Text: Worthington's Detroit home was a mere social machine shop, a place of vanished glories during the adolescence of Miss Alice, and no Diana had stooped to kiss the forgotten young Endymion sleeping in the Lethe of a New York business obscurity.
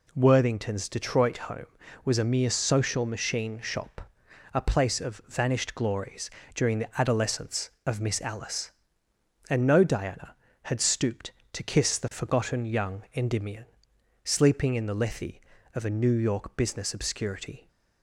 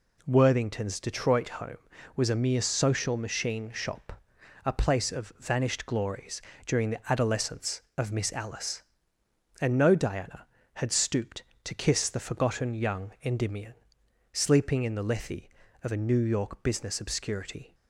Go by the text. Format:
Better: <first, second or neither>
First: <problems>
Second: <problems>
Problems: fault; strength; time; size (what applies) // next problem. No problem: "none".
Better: neither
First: pauses between "glories" and "during"; slight; at 6.2 s; 0.24 s long // pauses between "Endymion" and "sleeping"; noticeable; at 13.6 s; 0.58 s long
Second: pauses between "glories" and "during"; slight; at 6.4 s; 0.24 s long // pauses between "Endymion" and "sleeping"; noticeable; at 13.7 s; 0.58 s long